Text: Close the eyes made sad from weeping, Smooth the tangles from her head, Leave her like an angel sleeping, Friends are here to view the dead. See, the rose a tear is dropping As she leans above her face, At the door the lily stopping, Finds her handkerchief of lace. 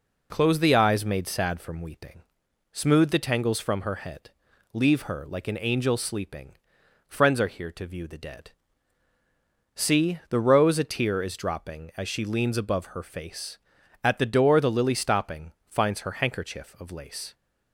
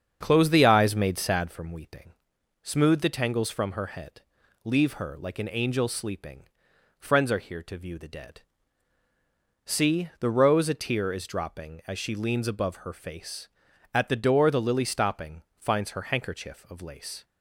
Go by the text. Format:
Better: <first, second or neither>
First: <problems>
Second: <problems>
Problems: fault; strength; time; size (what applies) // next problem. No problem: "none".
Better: first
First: none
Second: starts louder than the rest; strong; until 1.5 s; 7.5 dB